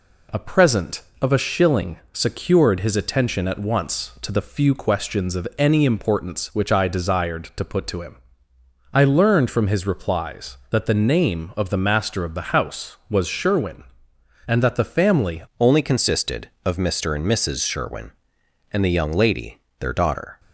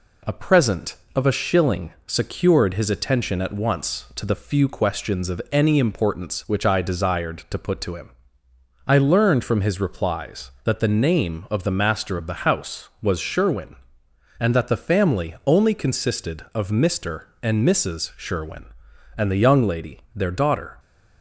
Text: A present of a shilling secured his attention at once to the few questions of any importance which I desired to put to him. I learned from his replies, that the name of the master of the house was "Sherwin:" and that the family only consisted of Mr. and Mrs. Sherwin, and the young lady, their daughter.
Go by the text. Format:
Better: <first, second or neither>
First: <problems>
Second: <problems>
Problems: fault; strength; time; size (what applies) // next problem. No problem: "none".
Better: second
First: changes voice at "only"; from 15.5 s on; 4.8 s long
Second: none